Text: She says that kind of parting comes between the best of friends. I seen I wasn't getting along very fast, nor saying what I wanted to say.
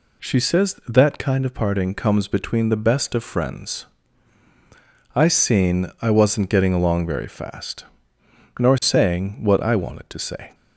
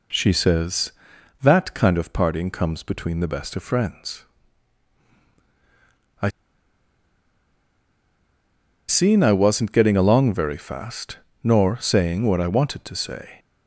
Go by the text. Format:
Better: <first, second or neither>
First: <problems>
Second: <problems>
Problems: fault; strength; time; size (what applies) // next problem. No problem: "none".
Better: first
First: none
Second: pauses between "I" and "seen"; strong; at 6.2 s; 2.5 s long